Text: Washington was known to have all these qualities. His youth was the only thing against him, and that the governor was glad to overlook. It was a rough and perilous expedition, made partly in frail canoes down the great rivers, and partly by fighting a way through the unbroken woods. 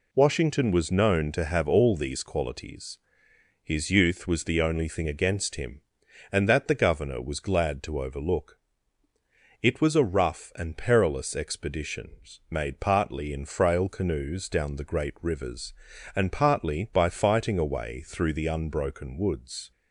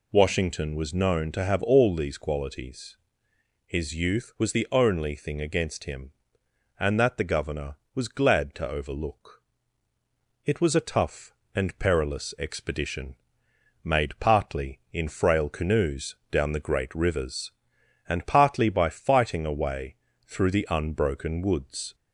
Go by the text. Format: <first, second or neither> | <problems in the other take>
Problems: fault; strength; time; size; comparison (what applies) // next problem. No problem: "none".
first | says "tough" for "rough"; at 10.8 s // pauses between "canoes" and "down"; slight; at 16.1 s; 0.16 s long // pauses between "way" and "through"; slight; at 19.9 s; 0.28 s long